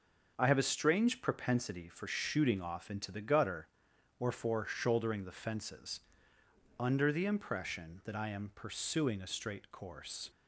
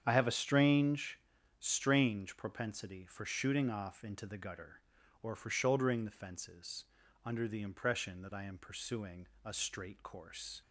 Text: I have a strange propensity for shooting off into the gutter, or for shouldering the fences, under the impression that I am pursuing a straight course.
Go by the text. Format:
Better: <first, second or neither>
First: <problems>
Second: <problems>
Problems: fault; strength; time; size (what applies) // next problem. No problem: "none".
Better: first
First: none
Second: starts louder than the rest; strong; until 1.0 s; 8 dB // says "strange" twice; at 1.6 s // pauses between "pursuing" and "a"; slight; at 9.2 s; 0.18 s long